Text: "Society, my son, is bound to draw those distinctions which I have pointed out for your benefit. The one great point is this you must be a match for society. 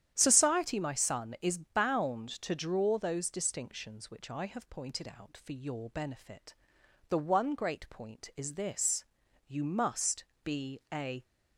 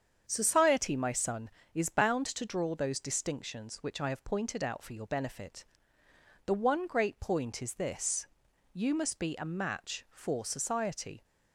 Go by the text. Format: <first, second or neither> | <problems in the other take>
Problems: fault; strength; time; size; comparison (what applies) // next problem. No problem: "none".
second | starts louder than the rest; strong; until 1.1 s; 10 dB; strong in the second // pauses between "this" and "you"; at 9.0 s; 0.44 s long; noticeable in the second // pauses between "must" and "be"; slight; at 10.2 s; 0.20 s long // stops before "match for society"; at 11.2 s